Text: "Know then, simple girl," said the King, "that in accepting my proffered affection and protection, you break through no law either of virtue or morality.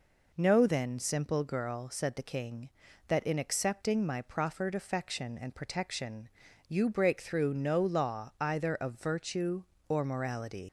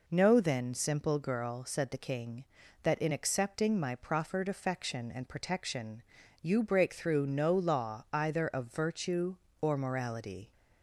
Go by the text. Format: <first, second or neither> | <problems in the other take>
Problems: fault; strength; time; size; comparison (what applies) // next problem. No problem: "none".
second | leaves "morality" unfinished; at 10.6 s; 100 ms